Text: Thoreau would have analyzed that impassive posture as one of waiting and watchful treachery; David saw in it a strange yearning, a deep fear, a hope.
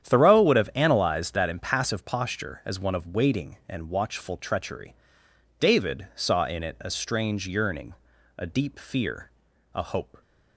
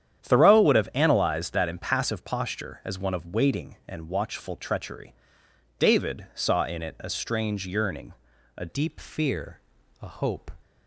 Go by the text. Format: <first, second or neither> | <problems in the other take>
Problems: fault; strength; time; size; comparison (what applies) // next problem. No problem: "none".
first | starts louder than the rest; strong; until 1.2 s; 9.5 dB; strong in the first // changes voice at "deep"; from 8.6 s on; 1.9 s long